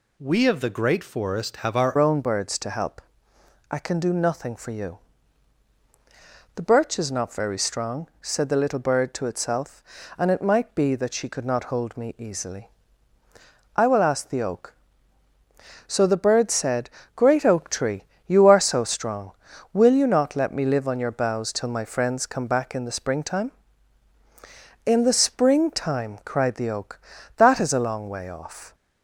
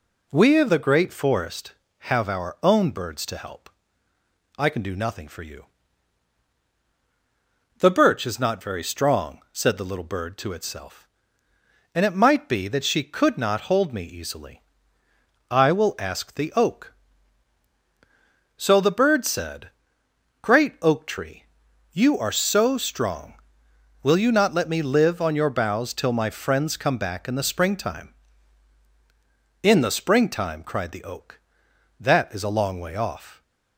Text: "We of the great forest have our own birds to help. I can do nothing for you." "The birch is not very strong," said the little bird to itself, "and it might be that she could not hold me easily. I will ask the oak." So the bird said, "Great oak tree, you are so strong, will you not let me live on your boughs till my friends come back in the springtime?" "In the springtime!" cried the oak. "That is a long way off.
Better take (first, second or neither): second